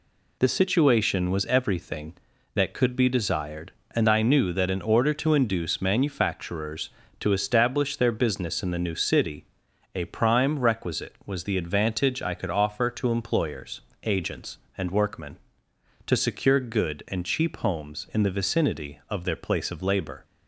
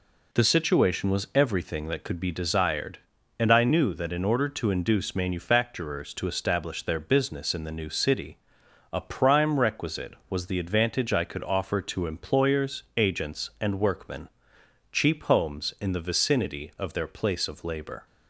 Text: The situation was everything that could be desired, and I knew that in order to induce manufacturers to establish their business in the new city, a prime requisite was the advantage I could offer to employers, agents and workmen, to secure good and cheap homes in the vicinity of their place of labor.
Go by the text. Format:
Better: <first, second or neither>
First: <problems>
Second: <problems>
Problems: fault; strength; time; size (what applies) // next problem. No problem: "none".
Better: first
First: none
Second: skips "to secure good and"; at 14.5 s